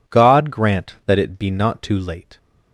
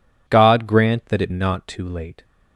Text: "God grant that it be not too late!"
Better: first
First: none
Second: skips "be"; at 1.3 s

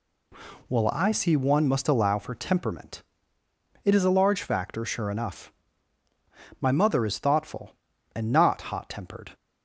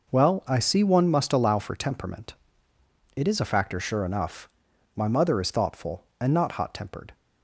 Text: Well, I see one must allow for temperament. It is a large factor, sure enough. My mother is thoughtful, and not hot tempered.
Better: first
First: none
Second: skips "large"; at 3.4 s

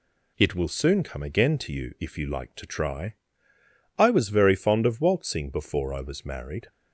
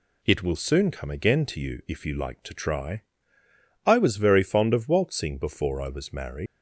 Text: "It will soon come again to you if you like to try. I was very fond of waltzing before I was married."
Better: first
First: none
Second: leaves "married" unfinished; at 6.4 s; 120 ms

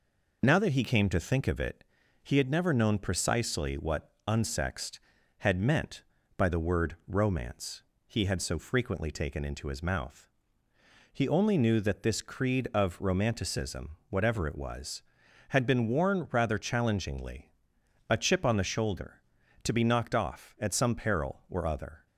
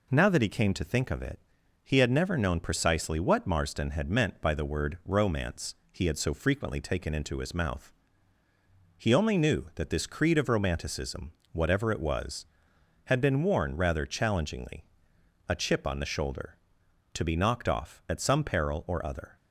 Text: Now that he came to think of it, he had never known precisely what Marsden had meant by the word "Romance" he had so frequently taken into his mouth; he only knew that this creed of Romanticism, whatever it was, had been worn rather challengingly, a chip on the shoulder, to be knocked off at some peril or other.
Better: second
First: says "Unsexed" for "Marsden"; at 4.2 s // pauses between "Romance" and "he"; slight; at 7.8 s; 0.26 s long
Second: pauses between "Romance" and "he"; slight; at 5.7 s; 0.18 s long

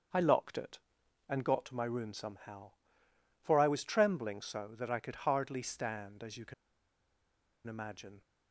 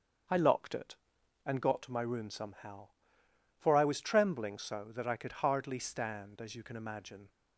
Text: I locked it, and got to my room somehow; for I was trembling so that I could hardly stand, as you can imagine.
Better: second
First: starts louder than the rest; until 1.6 s; 6.5 dB // pauses between "can" and "imagine"; at 6.5 s; 1.1 s long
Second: starts louder than the rest; until 1.8 s; 6.5 dB

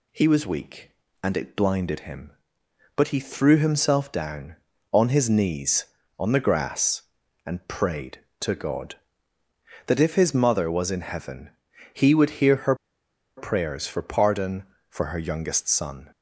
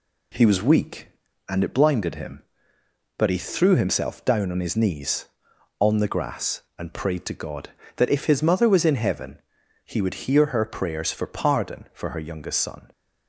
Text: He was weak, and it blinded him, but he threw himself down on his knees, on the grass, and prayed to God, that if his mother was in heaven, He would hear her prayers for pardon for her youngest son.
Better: second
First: pauses between "her" and "prayers"; noticeable; at 12.7 s; 0.62 s long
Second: none

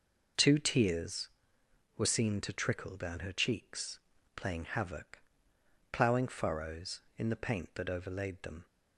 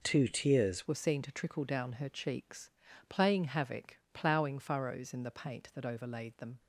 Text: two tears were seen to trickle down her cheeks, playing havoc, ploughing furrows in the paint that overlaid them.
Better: first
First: none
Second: changes voice at "were"; from 0.8 s on; 5.7 s long

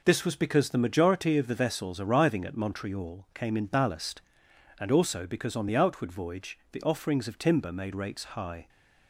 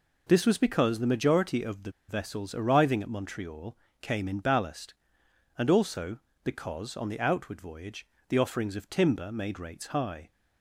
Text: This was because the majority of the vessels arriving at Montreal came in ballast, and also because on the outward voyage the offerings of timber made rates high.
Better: first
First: none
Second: pauses between "the" and "vessels"; slight; at 1.9 s; 0.17 s long // pauses between "Montreal" and "came"; slight; at 3.7 s; 0.24 s long // pauses between "voyage" and "the"; slight; at 8.0 s; 0.22 s long

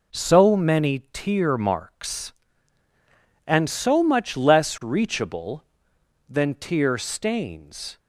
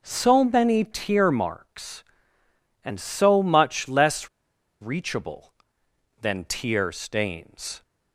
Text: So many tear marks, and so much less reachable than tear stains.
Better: first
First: none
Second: pauses between "less" and "reachable"; noticeable; at 4.2 s; 0.53 s long

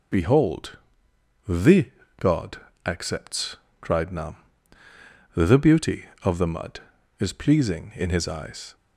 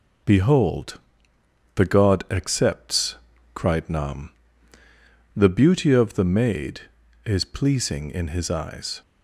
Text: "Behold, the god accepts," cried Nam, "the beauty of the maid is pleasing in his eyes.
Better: second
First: pauses between "the" and "god"; slight; at 1.9 s; 0.28 s long // pauses between "god" and "accepts"; slight; at 2.5 s; 0.26 s long // says "mud" for "maid"; at 6.4 s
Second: none

